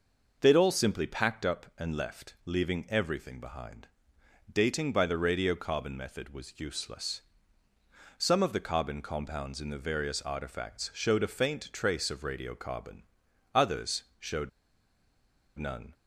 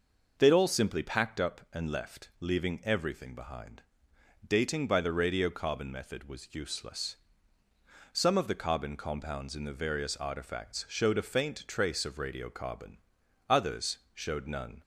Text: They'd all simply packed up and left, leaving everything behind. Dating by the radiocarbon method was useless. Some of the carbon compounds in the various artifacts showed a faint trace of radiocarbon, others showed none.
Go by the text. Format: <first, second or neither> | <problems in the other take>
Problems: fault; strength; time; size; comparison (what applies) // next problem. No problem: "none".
second | pauses between "others" and "showed"; slight; at 14.0 s; 0.16 s long; slight in the second // pauses between "showed" and "none"; at 14.4 s; 1.0 s long